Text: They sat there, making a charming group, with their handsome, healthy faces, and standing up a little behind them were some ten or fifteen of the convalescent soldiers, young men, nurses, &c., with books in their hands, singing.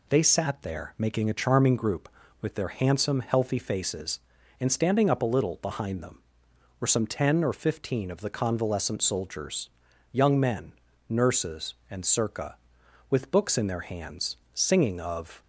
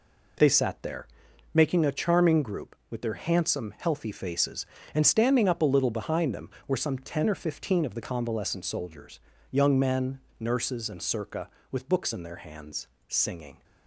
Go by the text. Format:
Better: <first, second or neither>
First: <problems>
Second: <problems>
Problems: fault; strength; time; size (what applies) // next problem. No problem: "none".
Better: second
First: goes on to say "Of"; slight; from 14.9 s on; 0.42 s long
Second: none